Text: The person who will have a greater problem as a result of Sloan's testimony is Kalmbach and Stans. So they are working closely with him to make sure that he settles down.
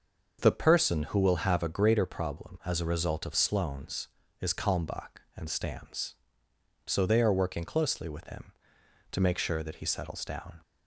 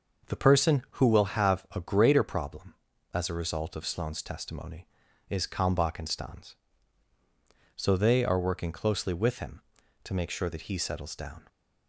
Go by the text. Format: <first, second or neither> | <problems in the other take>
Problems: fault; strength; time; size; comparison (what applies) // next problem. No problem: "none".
second | starts louder than the rest; until 1.4 s; 6.5 dB; noticeable in the second // skips "testimony"; at 4.2 s